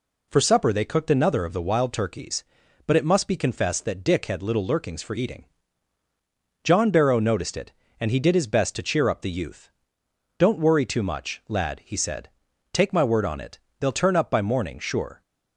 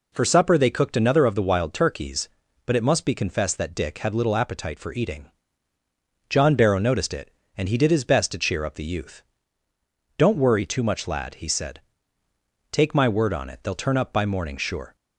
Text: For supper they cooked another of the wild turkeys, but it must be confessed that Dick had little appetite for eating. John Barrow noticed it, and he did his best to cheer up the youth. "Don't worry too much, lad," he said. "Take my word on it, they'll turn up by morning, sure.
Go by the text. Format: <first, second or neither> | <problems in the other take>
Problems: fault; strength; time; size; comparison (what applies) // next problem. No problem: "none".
second | says "lurkings" for "appetite"; at 4.6 s